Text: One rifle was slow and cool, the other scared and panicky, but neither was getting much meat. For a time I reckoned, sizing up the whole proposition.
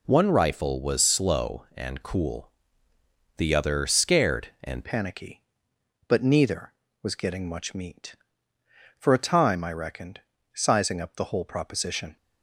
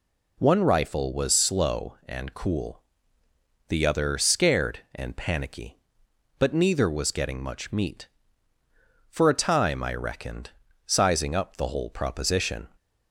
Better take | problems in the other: second | changes voice at "panicky"; from 4.8 s on; 7.3 s long

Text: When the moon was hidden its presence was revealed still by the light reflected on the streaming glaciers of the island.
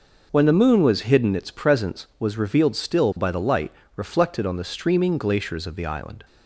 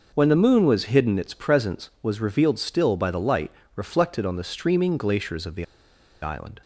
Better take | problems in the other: first | pauses between "light" and "reflected"; slight; at 3.5 s; 0.26 s long; slight in the first // pauses between "the" and "island"; noticeable; at 5.6 s; 0.57 s long

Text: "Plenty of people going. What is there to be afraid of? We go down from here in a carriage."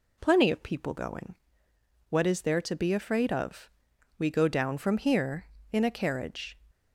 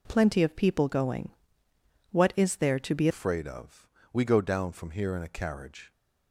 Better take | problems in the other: first | changes voice at "afraid"; from 3.0 s on; 2.9 s long

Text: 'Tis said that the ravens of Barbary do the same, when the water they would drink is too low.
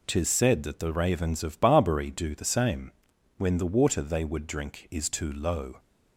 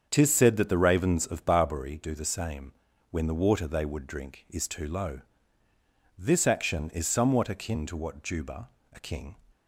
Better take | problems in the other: first | starts louder than the rest; until 1.1 s; 7 dB // goes on to say "This action is somewhat akin to what Juba a king"; strong; from 6.1 s on; 3.1 s long

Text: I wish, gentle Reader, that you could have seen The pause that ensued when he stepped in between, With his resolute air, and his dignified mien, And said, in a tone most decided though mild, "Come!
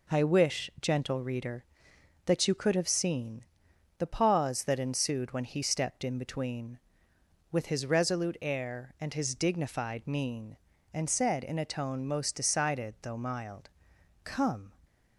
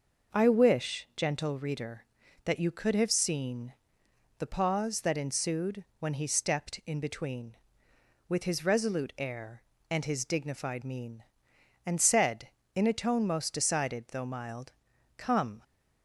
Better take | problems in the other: neither | pauses between "seen" and "The"; noticeable; the same in both

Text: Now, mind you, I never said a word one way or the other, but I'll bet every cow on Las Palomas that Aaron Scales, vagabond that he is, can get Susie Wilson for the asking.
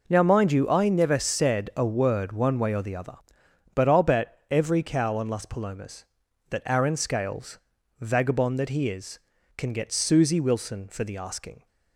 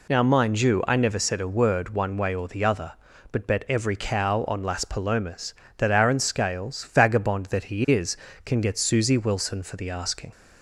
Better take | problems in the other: first | skips "I'll"; at 3.4 s

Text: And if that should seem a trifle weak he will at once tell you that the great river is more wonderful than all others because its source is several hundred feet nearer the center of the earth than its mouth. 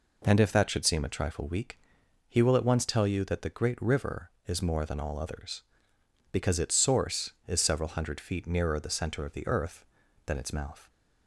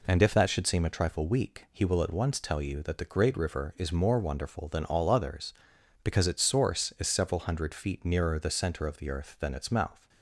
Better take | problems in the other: second | pauses between "weak" and "he"; noticeable; at 1.7 s; 0.52 s long // skips "wonderful"; at 4.8 s

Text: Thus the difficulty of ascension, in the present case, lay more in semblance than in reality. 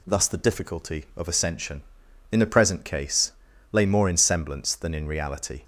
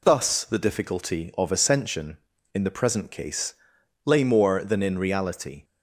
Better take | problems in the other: first | skips "in semblance"; at 4.6 s

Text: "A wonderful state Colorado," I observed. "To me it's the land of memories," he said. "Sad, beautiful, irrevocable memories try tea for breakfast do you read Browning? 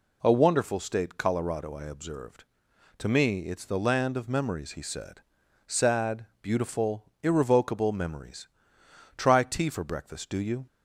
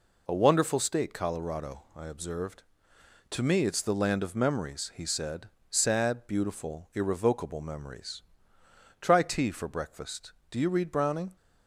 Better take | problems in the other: second | pauses between "memories" and "try"; noticeable; at 8.4 s; 0.70 s long; noticeable in the second // stops before "read Browning"; at 10.6 s

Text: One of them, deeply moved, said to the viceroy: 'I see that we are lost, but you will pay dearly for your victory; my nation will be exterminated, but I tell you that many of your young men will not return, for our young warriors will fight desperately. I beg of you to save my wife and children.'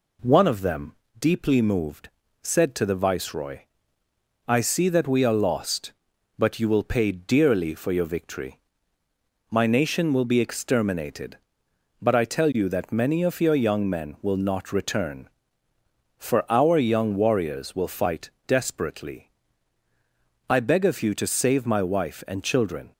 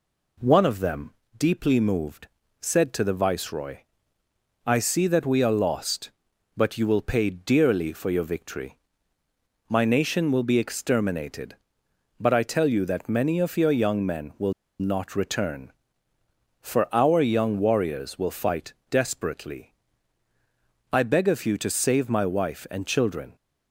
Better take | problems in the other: first | pauses between "will" and "not"; slight; at 14.5 s; 0.27 s long // pauses between "fight" and "desperately"; slight; at 18.7 s; 0.16 s long; slight in the first

